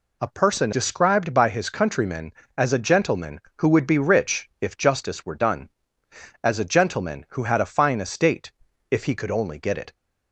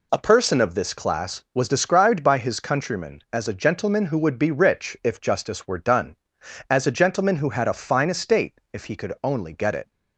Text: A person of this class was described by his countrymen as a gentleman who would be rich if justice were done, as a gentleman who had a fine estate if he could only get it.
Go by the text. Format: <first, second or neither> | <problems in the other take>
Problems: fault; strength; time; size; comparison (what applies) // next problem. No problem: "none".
second | skips "of this class was"; at 0.7 s // pauses between "estate" and "if"; at 8.5 s; 0.40 s long